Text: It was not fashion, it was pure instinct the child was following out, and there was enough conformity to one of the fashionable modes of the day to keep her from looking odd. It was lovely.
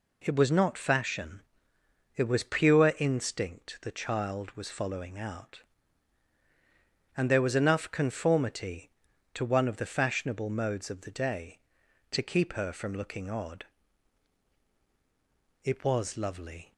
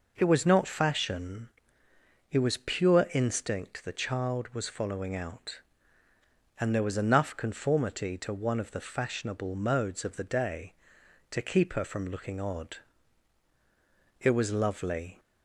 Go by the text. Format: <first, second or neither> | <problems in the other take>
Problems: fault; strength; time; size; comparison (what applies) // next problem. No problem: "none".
neither | none